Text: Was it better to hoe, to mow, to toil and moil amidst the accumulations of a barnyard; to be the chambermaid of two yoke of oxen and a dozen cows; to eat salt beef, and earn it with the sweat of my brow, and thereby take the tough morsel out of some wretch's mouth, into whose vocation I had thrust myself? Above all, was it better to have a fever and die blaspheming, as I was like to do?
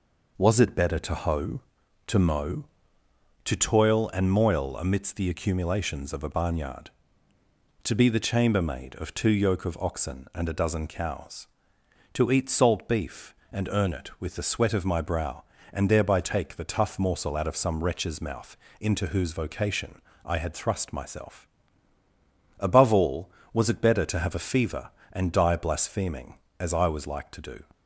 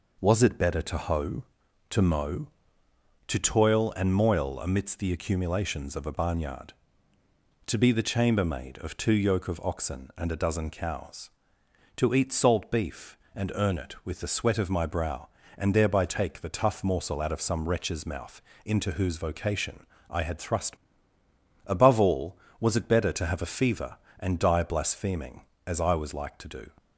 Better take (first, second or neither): first